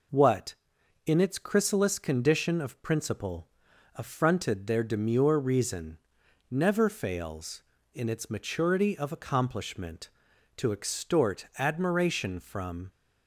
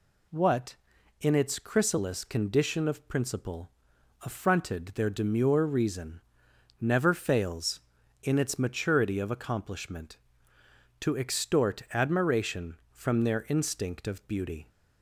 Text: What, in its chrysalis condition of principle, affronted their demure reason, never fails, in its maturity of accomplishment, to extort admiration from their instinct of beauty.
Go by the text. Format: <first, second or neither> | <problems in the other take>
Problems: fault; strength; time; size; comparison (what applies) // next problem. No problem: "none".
second | stops before "their instinct of beauty"; at 12.8 s